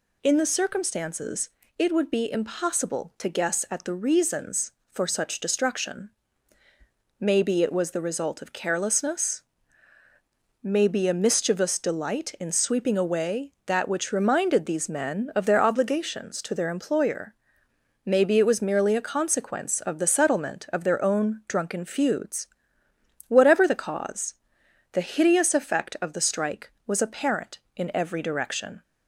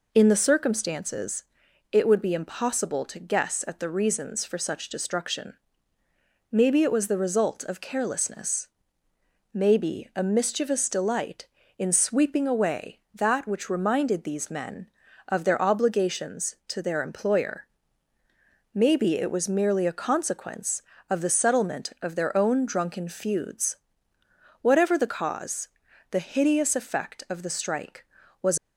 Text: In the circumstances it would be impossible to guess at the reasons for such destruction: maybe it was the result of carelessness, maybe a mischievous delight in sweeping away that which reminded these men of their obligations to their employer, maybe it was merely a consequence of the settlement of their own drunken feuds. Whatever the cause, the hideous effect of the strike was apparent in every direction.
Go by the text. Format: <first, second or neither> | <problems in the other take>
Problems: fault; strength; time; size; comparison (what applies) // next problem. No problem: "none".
first | pauses between "circumstances" and "it"; noticeable; at 1.4 s; 0.48 s long; slight in the first // stops before "apparent in every direction"; at 28.5 s